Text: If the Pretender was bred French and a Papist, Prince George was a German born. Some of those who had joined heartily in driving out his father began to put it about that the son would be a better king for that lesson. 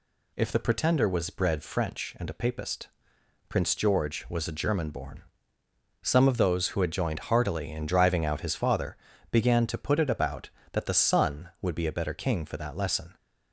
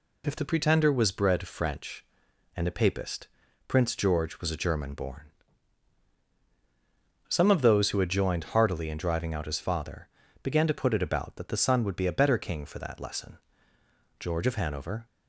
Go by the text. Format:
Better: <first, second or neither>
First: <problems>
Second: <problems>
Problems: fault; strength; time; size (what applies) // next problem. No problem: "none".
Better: first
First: pauses between "father" and "began"; slight; at 8.9 s; 0.34 s long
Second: pauses between "father" and "began"; slight; at 10.0 s; 0.34 s long // goes on to say "George of Hanover"; noticeable; from 14.1 s on; 0.86 s long